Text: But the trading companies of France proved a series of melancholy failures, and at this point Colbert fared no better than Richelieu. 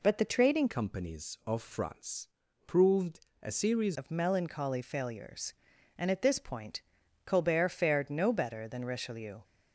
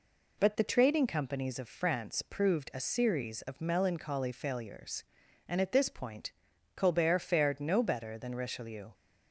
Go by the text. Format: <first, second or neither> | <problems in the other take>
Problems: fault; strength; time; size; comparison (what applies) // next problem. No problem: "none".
second | changes voice from "companies" to "series"; from 0.6 to 3.9 s; 3.3 s long // pauses between "France" and "proved"; slight; at 2.2 s; 0.36 s long // pauses between "proved" and "a"; slight; at 3.2 s; 0.22 s long // pauses between "point" and "Colbert"; at 6.8 s; 0.44 s long; also in the second